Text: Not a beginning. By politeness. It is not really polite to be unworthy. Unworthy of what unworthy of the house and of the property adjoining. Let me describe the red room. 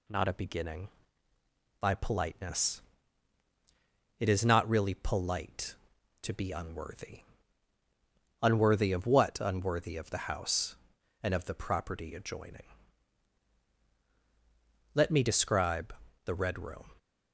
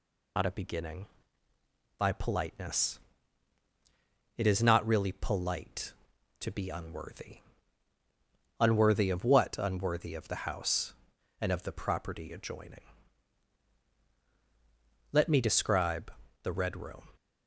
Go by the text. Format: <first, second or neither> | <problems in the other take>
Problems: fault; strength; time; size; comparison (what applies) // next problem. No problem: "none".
first | loses the start of "Not"; at 0.3 s; 95 ms // pauses between "describe" and "the"; slight; at 16.1 s; 0.32 s long; slight in the first